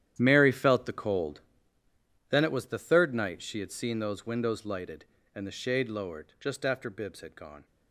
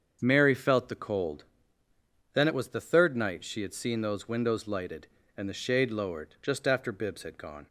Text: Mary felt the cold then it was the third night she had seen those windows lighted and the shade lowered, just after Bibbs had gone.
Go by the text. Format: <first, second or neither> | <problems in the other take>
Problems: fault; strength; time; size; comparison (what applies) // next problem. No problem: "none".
second | gets quieter; strong; throughout; 15 dB // starts louder than the rest; strong; until 1.2 s; 11 dB; also in the second // pauses between "cold" and "then"; noticeable; at 1.4 s; 0.88 s long; noticeable in the second